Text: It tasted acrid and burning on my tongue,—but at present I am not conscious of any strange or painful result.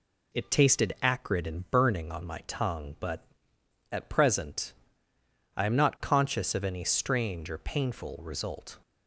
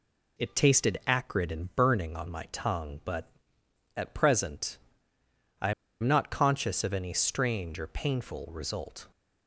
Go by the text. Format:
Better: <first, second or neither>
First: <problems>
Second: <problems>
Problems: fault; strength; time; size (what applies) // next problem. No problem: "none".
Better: first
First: pauses between "present" and "I"; noticeable; at 4.7 s; 0.82 s long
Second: pauses between "present" and "I"; noticeable; at 4.7 s; 0.82 s long // pauses between "I" and "am"; slight; at 5.7 s; 0.29 s long